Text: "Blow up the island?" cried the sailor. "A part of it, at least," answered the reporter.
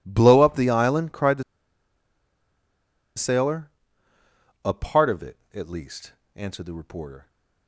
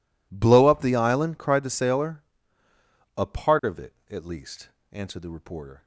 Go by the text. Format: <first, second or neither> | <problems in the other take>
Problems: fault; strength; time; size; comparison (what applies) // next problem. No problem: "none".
second | pauses between "the" and "sailor"; strong; at 1.4 s; 1.7 s long